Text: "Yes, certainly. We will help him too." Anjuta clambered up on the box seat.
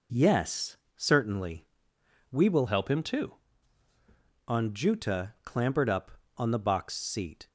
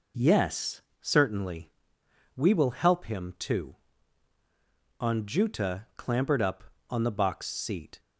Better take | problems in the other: second | changes voice from "help" to "too"; from 2.6 to 3.3 s; 0.7 s long

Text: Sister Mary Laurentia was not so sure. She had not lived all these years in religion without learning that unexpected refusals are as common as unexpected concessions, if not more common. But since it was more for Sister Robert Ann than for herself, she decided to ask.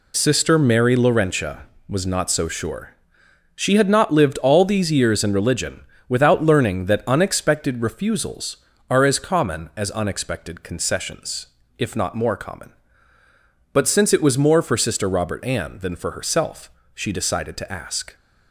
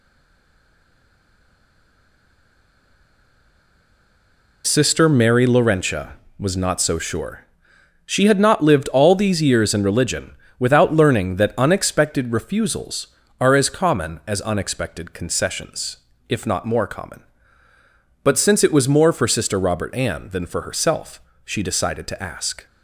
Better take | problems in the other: first | stays silent before the first word; strong; until 4.6 s; 4.6 s long // pauses between "religion" and "without"; slight; at 10.3 s; 0.24 s long; slight in the first

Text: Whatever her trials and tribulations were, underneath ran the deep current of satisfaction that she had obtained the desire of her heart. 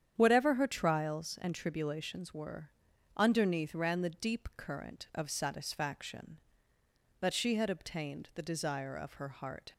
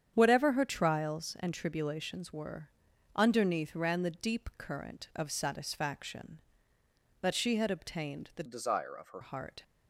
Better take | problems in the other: first | starts louder than the rest; strong; until 1.1 s; 8.5 dB; strong in the first // changes voice from "desire" to "her"; from 8.4 to 9.2 s; 0.8 s long

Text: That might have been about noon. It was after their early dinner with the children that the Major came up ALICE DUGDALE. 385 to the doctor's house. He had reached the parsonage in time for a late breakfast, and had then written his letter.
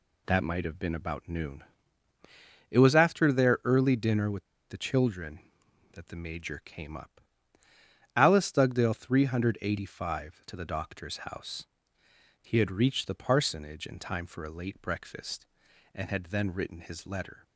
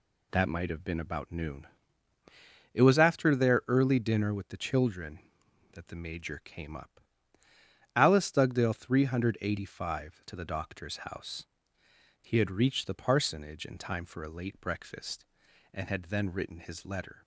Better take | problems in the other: second | pauses between "with" and "the"; slight; at 4.4 s; 0.23 s long // pauses between "up" and "ALICE"; noticeable; at 7.1 s; 0.96 s long; noticeable in the second

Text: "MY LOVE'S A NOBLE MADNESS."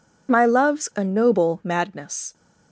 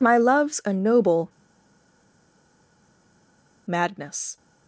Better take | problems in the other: first | pauses between "NOBLE" and "MADNESS"; strong; at 1.2 s; 2.3 s long

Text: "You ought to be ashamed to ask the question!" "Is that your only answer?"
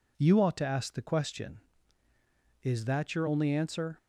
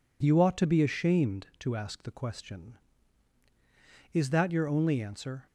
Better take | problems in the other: second | skips "be ashamed to"; at 0.6 s

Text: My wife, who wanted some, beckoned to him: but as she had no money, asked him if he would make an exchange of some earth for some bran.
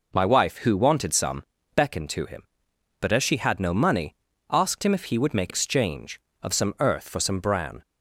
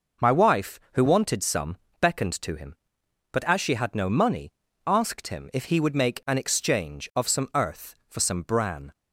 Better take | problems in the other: second | skips "an"; at 5.5 s

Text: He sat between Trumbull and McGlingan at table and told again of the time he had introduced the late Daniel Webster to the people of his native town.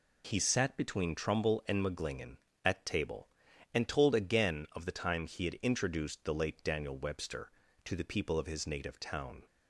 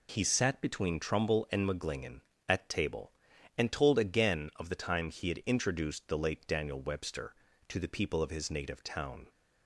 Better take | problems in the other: neither | none

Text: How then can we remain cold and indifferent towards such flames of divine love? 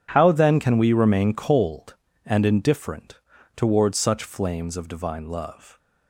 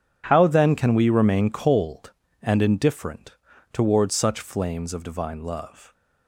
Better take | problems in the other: neither | pauses between "indifferent" and "towards"; slight; the same in both

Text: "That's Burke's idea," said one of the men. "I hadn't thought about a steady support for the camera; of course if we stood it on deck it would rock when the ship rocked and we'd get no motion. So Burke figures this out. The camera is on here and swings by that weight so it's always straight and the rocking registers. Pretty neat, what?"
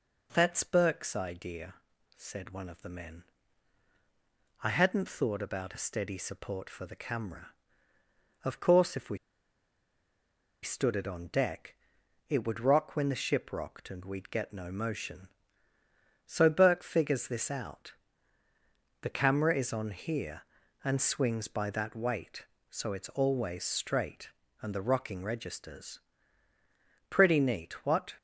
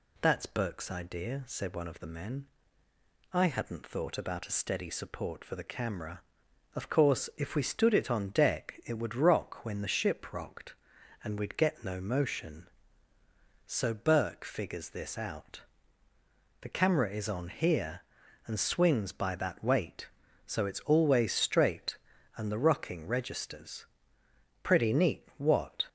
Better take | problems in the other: second | pauses between "we" and "stood"; strong; at 9.1 s; 1.4 s long // pauses between "deck" and "it"; noticeable; at 11.7 s; 0.54 s long

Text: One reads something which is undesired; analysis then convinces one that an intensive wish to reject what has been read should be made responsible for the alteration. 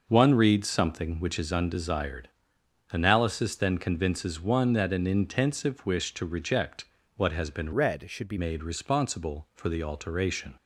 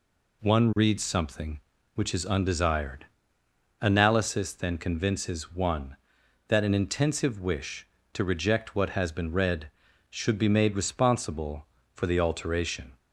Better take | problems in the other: second | pauses between "reject" and "what"; slight; at 6.8 s; 0.32 s long // changes voice from "read" to "be"; from 7.7 to 8.3 s; 0.6 s long

